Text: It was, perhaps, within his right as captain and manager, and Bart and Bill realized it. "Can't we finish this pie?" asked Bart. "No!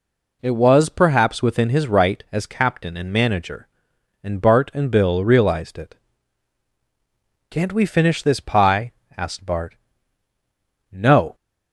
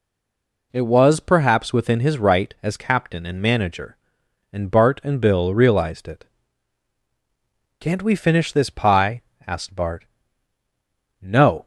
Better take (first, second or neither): first